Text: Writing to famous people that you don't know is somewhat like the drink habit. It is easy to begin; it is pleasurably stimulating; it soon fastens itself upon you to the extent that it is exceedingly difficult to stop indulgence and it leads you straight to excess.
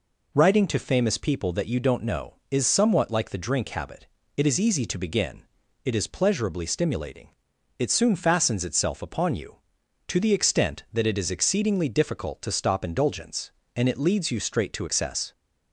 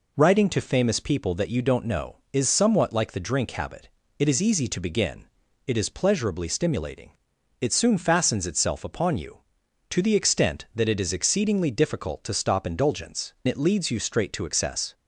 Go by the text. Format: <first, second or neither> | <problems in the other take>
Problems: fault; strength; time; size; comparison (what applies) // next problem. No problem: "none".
first | skips "and"; at 13.3 s